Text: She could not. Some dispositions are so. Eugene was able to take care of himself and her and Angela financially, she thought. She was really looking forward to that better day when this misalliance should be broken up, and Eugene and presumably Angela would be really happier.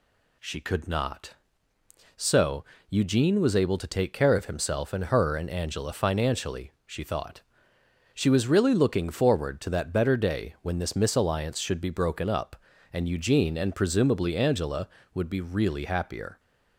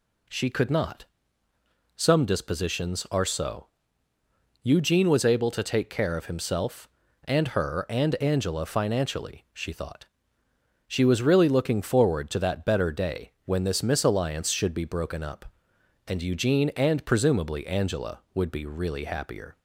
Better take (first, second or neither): second